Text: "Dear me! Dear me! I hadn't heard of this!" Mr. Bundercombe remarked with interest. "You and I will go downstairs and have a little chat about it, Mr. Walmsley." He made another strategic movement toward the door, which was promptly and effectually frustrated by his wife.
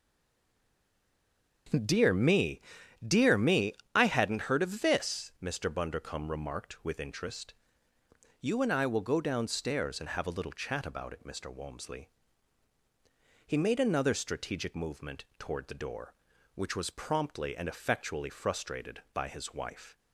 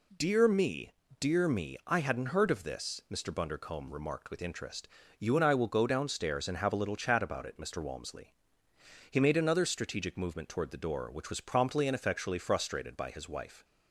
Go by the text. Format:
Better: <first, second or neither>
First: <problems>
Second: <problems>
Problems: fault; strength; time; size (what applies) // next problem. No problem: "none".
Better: second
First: stays silent before the first word; noticeable; until 1.6 s; 1.6 s long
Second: none